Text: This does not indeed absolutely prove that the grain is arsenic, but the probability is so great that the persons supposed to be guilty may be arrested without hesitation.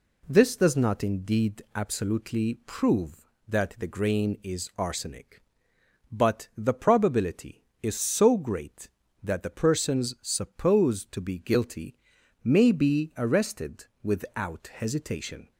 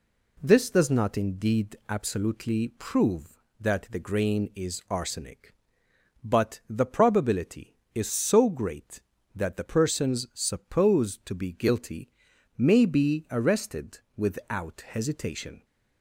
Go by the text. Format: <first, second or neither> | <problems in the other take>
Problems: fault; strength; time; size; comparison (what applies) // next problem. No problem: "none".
neither | pauses between "guilty" and "may"; noticeable; the same in both // pauses between "arrested" and "without"; slight; the same in both